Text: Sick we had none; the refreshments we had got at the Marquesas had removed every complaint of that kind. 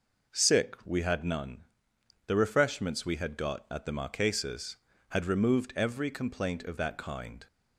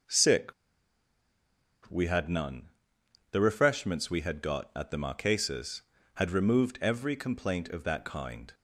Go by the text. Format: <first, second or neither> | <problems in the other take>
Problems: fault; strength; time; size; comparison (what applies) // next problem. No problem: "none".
first | pauses between "Sick" and "we"; strong; at 0.5 s; 1.3 s long